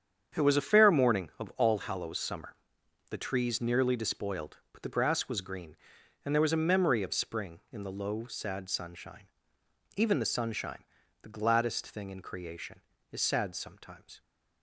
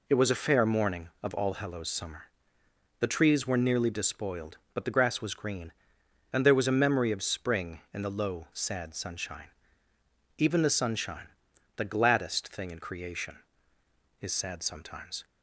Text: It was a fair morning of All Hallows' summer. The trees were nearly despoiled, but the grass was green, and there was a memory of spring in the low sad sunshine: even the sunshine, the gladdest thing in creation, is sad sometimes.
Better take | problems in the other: second | starts louder than the rest; strong; until 1.4 s; 8 dB // skips "were"; at 3.6 s

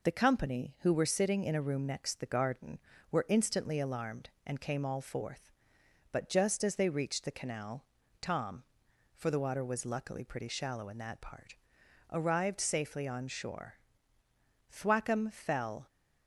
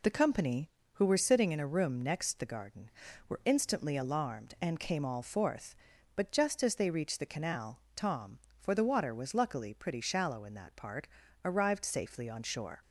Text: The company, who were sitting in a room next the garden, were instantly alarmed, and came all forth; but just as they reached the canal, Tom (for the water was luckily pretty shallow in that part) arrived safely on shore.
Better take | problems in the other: second | goes on to say "Thwackum fell"; noticeable; from 14.7 s on; 1.1 s long

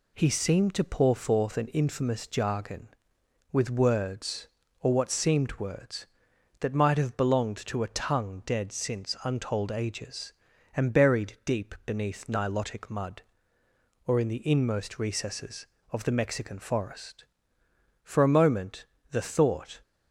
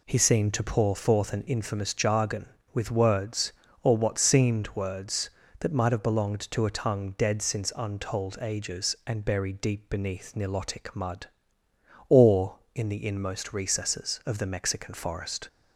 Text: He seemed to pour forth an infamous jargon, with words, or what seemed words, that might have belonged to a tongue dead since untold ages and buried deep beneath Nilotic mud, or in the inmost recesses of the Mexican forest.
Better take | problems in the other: second | goes on to say "For a moment the thought"; strong; from 18.0 s on; 1.7 s long

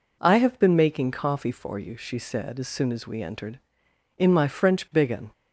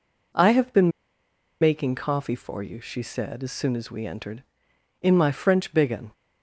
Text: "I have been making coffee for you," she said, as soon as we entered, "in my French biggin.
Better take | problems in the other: first | pauses between "been" and "making"; noticeable; at 0.8 s; 0.72 s long

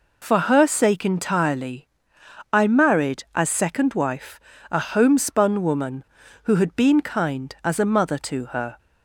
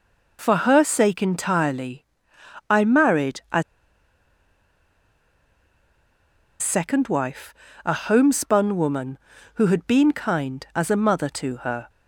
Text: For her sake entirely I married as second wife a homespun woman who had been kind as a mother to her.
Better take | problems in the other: first | pauses between "entirely" and "I"; noticeable; at 2.0 s; 0.64 s long; noticeable in the first // pauses between "as" and "second"; strong; at 3.6 s; 2.9 s long // pauses between "wife" and "a"; slight; at 7.5 s; 0.32 s long; slight in the first

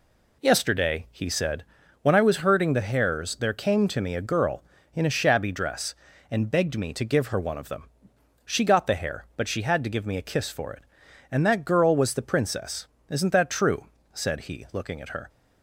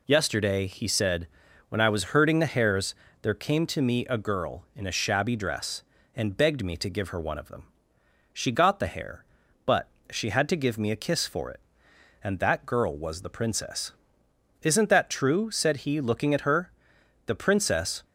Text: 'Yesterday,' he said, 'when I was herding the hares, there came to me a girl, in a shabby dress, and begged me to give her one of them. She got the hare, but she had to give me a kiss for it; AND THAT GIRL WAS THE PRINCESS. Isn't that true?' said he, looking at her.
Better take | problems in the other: first | pauses between "but" and "she"; slight; at 9.8 s; 0.22 s long // goes on to say "The princess"; noticeable; from 17.2 s on; 0.80 s long

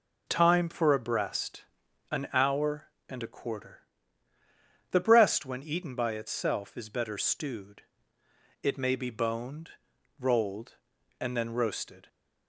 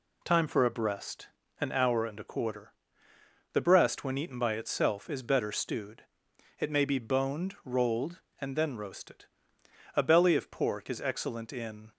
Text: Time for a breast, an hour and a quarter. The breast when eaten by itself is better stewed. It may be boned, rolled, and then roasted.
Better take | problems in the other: first | goes on to say "A belly of pork is excellent in"; strong; from 9.9 s on; 1.9 s long

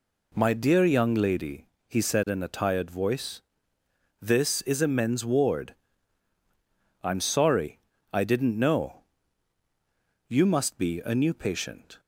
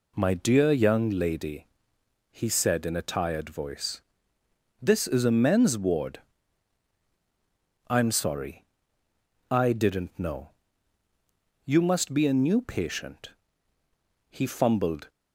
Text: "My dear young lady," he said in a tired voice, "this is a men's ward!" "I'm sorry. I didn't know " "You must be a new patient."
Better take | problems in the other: first | goes on to say "He fumbled"; noticeable; from 14.2 s on; 0.80 s long

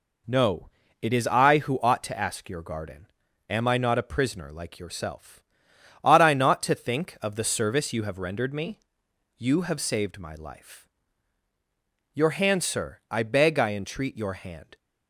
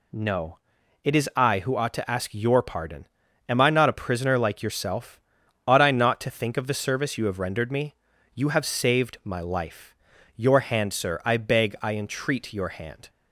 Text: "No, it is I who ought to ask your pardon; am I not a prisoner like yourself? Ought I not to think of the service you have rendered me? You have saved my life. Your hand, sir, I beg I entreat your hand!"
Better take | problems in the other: second | says "garden" for "pardon"; at 2.6 s

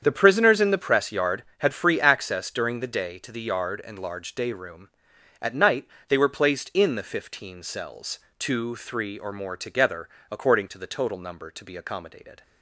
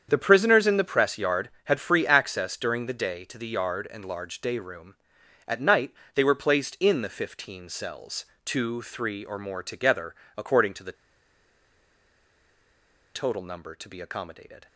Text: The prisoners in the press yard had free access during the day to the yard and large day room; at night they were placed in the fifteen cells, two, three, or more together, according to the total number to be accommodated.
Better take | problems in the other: first | starts louder than the rest; strong; until 1.1 s; 8 dB; strong in the first // pauses between "night" and "they"; slight; at 5.9 s; 0.22 s long; slight in the first // pauses between "the" and "total"; strong; at 10.9 s; 2.2 s long

